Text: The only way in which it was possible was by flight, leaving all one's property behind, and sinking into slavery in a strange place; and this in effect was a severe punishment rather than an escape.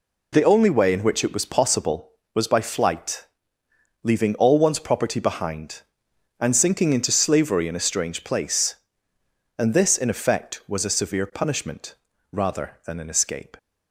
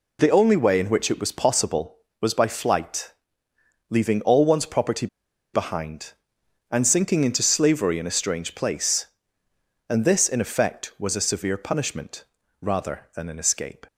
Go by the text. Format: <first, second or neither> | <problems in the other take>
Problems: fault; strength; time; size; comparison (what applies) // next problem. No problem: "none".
first | pauses between "property" and "behind"; noticeable; at 5.0 s; 0.47 s long // pauses between "punishment" and "rather"; at 12.2 s; 0.38 s long; also in the first